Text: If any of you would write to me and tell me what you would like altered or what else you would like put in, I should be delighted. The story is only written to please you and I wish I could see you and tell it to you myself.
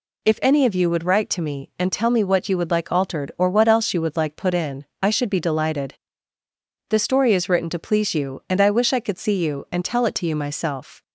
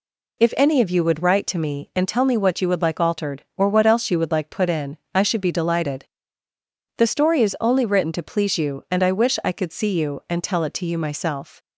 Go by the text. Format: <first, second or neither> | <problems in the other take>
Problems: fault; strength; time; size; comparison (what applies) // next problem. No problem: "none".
second | skips "only"; at 7.4 s